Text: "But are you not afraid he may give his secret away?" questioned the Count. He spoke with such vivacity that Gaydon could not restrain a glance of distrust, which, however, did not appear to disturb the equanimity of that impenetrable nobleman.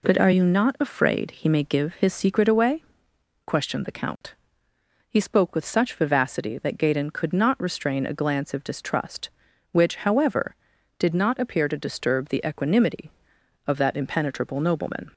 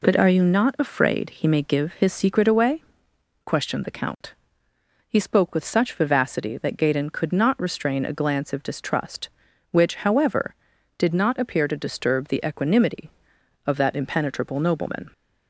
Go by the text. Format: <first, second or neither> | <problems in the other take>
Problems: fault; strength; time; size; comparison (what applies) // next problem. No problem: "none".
neither | none